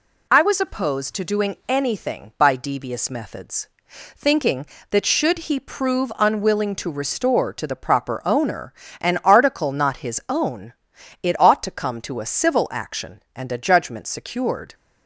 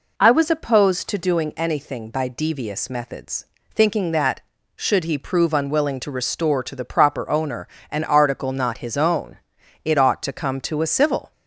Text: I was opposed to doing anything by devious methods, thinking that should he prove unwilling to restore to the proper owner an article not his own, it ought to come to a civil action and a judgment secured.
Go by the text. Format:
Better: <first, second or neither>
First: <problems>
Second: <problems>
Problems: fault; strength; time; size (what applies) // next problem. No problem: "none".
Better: first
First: pauses between "owner" and "an"; slight; at 8.7 s; 0.26 s long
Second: pauses between "owner" and "an"; slight; at 7.6 s; 0.24 s long // stops before "action and a judgment secured"; at 11.3 s